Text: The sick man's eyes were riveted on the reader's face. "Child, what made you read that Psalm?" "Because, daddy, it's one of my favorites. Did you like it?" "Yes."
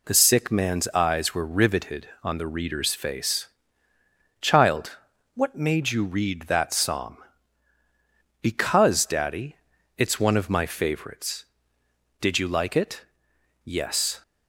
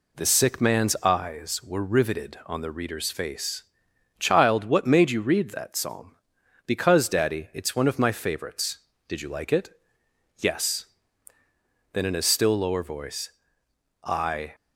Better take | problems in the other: first | goes on to say "Then in a still lower voice I"; strong; from 11.9 s on; 2.6 s long

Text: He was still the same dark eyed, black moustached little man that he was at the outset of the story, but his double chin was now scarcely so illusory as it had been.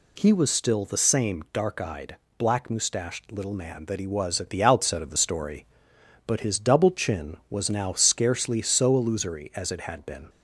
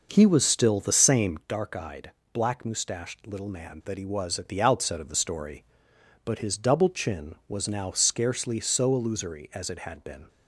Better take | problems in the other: first | starts louder than the rest; noticeable; until 1.4 s; 5.5 dB

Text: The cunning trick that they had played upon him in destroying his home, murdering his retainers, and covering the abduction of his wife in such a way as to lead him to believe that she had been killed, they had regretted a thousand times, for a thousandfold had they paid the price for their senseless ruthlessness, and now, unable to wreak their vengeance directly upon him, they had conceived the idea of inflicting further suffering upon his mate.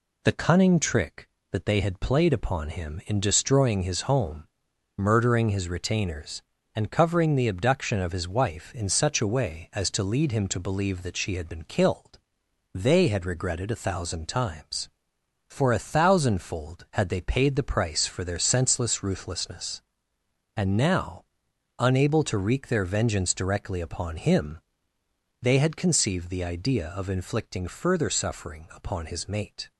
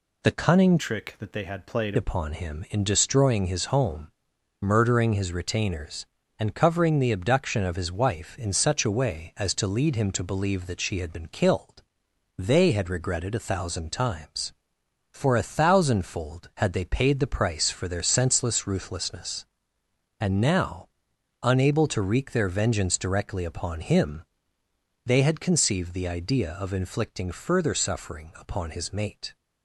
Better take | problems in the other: first | changes voice from "trick" to "played"; from 0.7 to 1.9 s; 1.2 s long

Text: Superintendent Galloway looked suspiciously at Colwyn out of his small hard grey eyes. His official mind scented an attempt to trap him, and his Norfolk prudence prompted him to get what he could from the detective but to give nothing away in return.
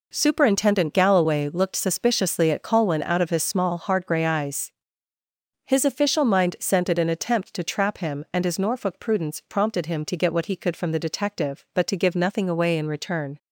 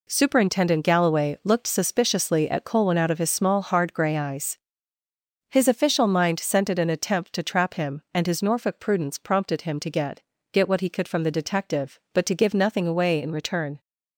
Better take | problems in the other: first | says "get" twice; at 10.5 s

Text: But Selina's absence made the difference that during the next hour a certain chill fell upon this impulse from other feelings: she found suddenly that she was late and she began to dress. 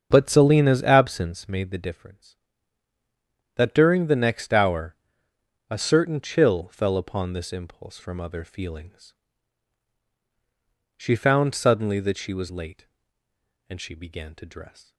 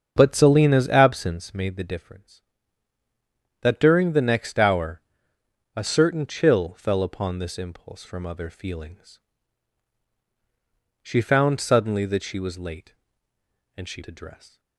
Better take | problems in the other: first | starts louder than the rest; until 1.1 s; 7 dB; also in the first // pauses between "hour" and "a"; noticeable; at 4.9 s; 0.76 s long; noticeable in the first // skips "began"; at 14.0 s

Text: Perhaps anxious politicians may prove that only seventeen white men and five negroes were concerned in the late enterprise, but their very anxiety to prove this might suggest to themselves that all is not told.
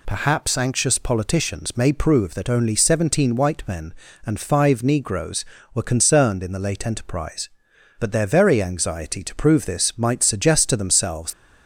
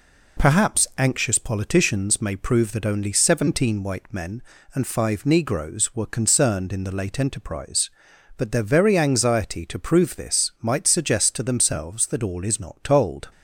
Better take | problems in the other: second | stops before "that all is not told"; at 11.3 s

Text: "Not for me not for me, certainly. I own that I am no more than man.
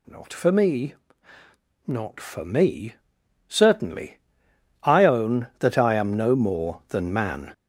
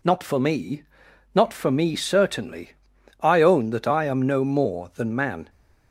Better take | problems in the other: second | gets louder; throughout; 7 dB // pauses between "me" and "not"; noticeable; at 0.9 s; 0.92 s long; noticeable in the second

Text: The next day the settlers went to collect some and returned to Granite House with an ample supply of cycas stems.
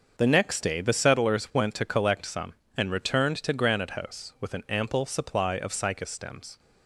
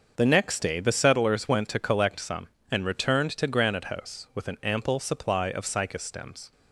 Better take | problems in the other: neither | starts louder than the rest; the same in both

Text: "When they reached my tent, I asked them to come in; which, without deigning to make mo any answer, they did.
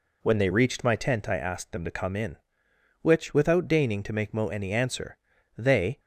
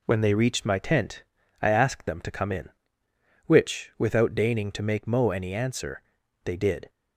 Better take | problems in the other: second | stops before "did"; at 5.9 s

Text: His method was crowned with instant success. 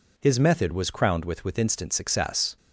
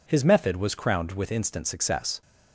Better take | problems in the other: second | says "with" twice; at 1.4 s

